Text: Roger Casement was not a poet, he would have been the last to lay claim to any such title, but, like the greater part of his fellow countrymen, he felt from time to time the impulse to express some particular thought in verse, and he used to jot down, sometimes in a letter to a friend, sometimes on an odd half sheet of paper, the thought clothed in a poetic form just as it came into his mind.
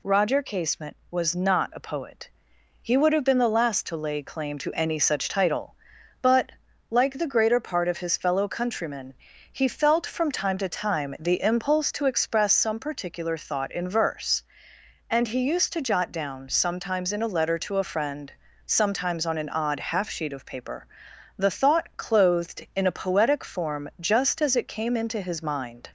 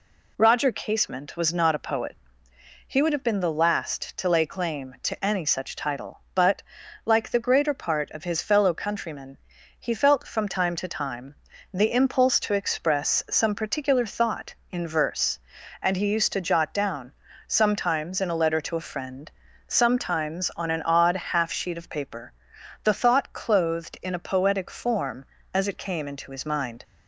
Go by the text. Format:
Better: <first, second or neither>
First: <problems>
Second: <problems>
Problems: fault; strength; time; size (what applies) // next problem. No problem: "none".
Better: first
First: none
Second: pauses between "time" and "the"; at 11.3 s; 0.40 s long // skips "just"; at 25.3 s